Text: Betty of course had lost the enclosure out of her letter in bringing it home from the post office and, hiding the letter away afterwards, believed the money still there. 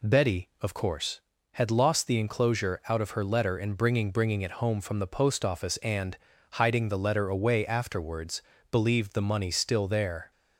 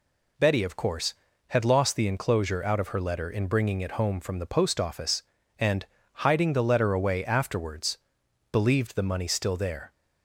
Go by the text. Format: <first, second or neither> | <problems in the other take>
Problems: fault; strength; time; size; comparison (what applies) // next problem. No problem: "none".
second | says "bringing" twice; at 4.1 s